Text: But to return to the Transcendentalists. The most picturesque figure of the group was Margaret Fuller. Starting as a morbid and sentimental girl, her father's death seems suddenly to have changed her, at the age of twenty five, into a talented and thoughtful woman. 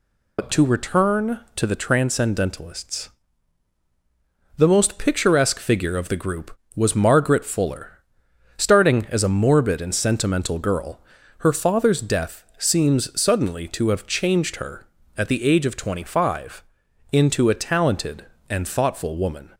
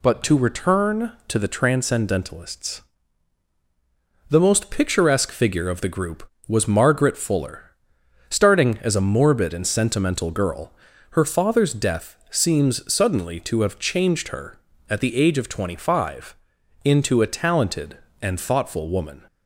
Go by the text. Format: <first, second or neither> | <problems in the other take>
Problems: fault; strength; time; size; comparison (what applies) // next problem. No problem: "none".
second | loses the start of "But"; at 0.3 s; 85 ms